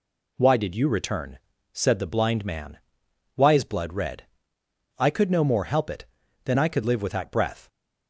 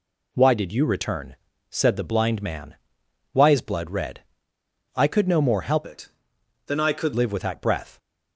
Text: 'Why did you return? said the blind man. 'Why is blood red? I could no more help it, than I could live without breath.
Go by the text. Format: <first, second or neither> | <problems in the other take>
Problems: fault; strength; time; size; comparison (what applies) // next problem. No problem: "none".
first | changes voice from "it" to "could"; from 5.8 to 7.1 s; 1.3 s long